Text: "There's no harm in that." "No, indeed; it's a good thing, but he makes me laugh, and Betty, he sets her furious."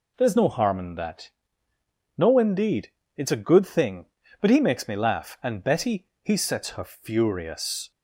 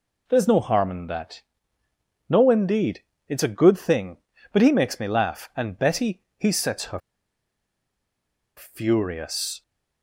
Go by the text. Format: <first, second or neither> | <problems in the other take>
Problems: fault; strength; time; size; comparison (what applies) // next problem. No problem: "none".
first | pauses between "her" and "furious"; strong; at 6.9 s; 1.5 s long